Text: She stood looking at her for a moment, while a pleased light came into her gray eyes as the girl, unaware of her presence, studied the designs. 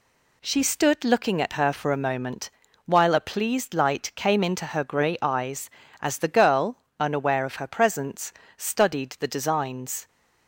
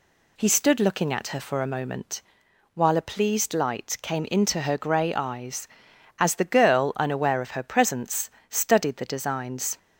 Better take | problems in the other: first | says "He" for "She"; at 0.3 s

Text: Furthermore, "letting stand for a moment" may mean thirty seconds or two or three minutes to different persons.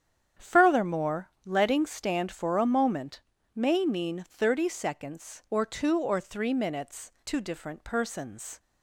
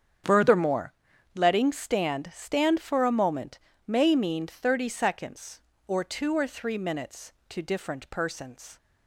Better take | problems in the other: first | starts louder than the rest; strong; until 1.6 s; 8 dB; strong in the first // says "stand" twice; at 2.3 s // pauses between "moment" and "may"; slight; at 3.5 s; 0.26 s long; slight in the first

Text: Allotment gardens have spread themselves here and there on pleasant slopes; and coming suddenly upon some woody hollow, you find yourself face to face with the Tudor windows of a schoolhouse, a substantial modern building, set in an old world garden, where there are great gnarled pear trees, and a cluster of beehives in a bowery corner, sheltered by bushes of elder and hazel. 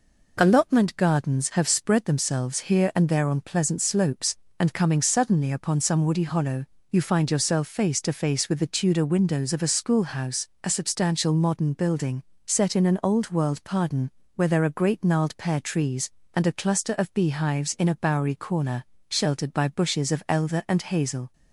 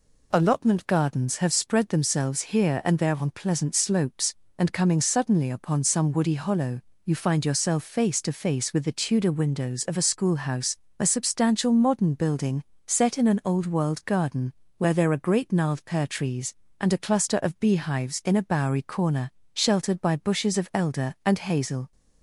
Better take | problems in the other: second | says "pardon" for "garden"; at 13.6 s

